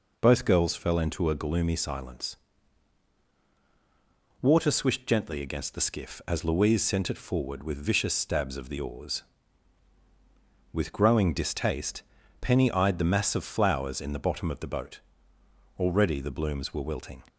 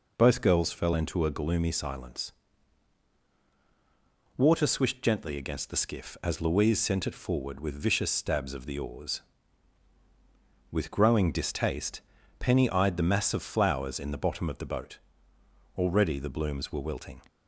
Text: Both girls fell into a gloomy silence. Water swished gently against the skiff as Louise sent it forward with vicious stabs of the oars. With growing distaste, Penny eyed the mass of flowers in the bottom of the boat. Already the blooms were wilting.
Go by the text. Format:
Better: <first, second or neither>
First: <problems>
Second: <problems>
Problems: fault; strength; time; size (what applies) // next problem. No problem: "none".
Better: neither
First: none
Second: none